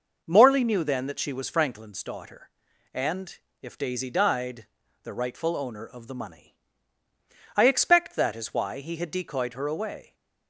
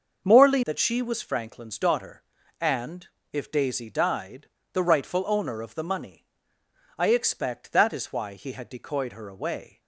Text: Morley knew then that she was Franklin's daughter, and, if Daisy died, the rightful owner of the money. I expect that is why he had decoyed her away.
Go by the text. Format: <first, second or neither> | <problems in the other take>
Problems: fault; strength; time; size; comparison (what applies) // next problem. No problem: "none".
first | starts louder than the rest; until 1.2 s; 6 dB // skips "knew then"; at 0.6 s